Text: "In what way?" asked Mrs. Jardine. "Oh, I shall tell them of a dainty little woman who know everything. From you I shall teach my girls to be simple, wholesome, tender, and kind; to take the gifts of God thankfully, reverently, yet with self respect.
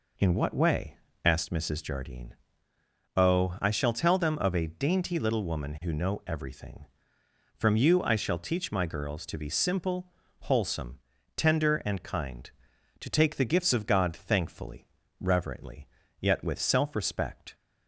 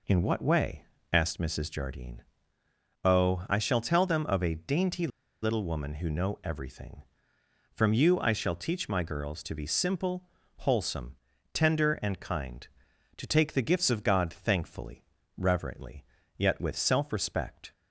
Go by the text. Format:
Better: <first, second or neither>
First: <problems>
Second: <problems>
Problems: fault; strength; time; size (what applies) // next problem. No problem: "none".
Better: first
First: none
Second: pauses between "dainty" and "little"; slight; at 5.0 s; 0.35 s long